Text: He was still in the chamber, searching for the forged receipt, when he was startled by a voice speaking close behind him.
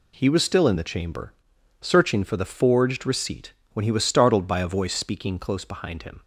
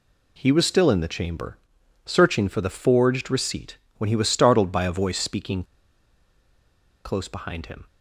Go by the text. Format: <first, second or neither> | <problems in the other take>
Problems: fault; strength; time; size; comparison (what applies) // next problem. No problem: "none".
first | pauses between "speaking" and "close"; strong; at 5.6 s; 1.4 s long